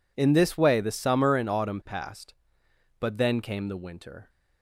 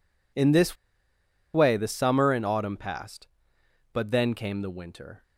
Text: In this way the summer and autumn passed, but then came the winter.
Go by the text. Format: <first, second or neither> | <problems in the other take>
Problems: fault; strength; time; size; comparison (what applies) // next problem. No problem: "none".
first | pauses between "this" and "way"; noticeable; at 0.7 s; 0.78 s long